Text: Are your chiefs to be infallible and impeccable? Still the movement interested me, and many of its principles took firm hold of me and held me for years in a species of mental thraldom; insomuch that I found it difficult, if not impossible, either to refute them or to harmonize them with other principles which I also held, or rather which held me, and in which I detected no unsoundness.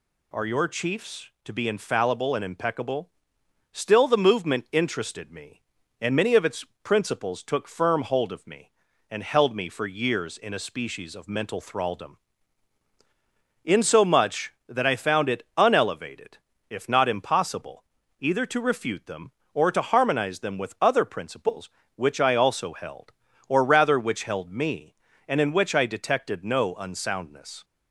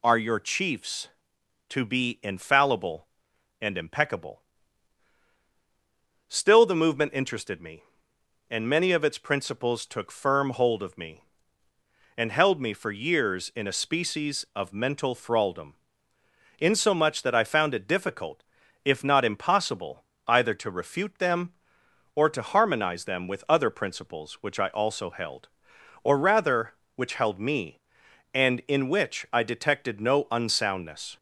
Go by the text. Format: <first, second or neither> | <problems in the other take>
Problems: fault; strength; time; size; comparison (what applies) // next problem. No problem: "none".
second | pauses between "its" and "principles"; slight; at 6.6 s; 0.18 s long // says "unelevated" for "difficult"; at 15.5 s